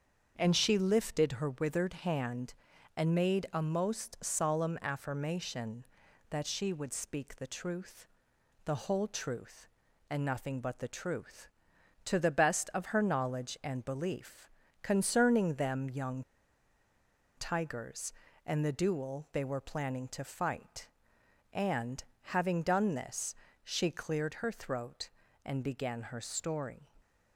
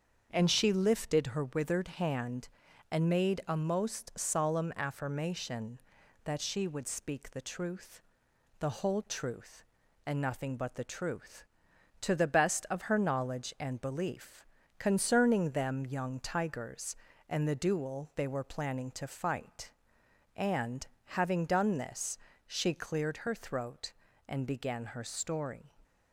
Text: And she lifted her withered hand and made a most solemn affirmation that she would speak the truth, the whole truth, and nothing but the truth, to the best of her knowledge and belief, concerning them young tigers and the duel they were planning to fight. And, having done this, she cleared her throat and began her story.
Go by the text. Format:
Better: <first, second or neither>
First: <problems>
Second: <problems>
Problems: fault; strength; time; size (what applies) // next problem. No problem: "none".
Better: second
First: starts louder than the rest; until 1.3 s; 7 dB // pauses between "young" and "tigers"; at 16.2 s; 1.1 s long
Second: starts louder than the rest; until 1.3 s; 7 dB